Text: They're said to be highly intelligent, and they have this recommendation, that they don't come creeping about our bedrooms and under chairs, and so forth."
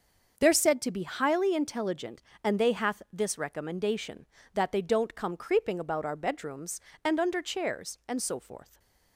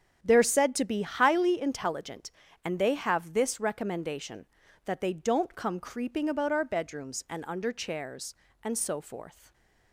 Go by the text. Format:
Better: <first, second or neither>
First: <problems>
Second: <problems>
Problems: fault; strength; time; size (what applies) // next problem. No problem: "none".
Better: second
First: starts louder than the rest; until 1.3 s; 6.5 dB // says "hath" for "have"; at 2.7 s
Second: starts louder than the rest; strong; until 1.2 s; 8 dB